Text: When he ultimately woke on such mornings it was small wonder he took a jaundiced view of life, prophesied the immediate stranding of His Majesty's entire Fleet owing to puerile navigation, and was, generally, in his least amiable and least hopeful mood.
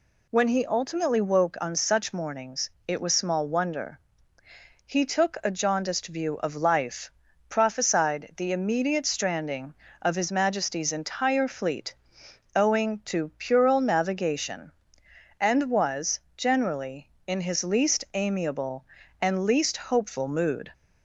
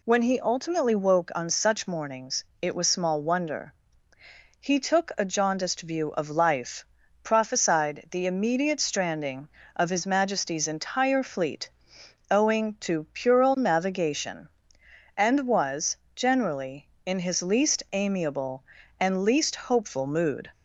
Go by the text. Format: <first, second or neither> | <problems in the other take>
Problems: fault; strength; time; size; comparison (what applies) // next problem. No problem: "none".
neither | pauses between "mornings" and "it"; slight; the same in both // pauses between "wonder" and "he"; noticeable; the same in both // pauses between "Fleet" and "owing"; noticeable; the same in both